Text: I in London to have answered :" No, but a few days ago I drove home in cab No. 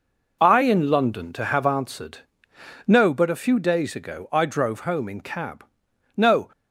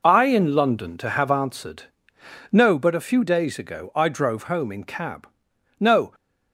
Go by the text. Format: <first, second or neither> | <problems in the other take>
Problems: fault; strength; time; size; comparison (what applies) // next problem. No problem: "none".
neither | pauses between "cab" and "No"; noticeable; the same in both